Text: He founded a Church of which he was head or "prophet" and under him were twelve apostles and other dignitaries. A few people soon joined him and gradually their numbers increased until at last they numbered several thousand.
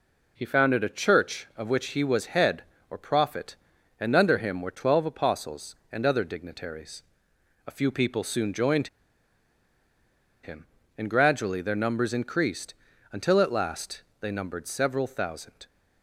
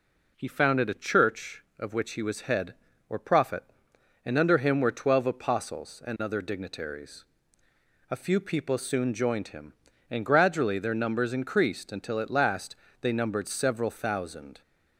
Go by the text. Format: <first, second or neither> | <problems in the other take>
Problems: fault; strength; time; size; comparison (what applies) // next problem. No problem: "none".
second | pauses between "joined" and "him"; strong; at 8.8 s; 1.5 s long // pauses between "increased" and "until"; slight; at 12.7 s; 0.36 s long // pauses between "last" and "they"; slight; at 14.0 s; 0.18 s long; slight in the second